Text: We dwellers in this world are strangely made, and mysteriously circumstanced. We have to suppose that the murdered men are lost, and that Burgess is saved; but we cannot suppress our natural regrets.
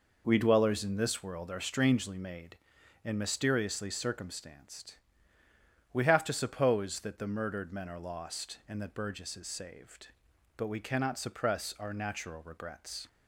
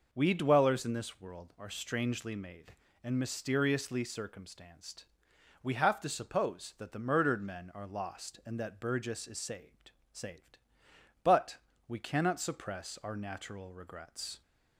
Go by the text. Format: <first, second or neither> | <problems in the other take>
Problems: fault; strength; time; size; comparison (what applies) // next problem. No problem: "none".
first | says "saved" twice; at 10.1 s // pauses between "but" and "we"; slight; at 11.5 s; 0.28 s long